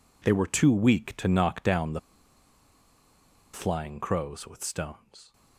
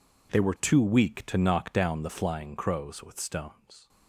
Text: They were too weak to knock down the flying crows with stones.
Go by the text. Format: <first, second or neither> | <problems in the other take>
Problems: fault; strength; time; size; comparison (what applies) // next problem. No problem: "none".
second | pauses between "the" and "flying"; strong; at 1.9 s; 1.5 s long